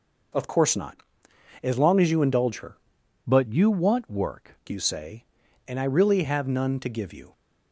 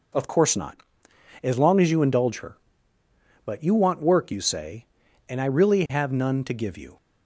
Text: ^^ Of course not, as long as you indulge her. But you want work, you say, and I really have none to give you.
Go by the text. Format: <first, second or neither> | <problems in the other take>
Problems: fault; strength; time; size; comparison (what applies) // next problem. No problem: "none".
second | changes voice from "But" to "work"; from 3.2 to 4.5 s; 1.3 s long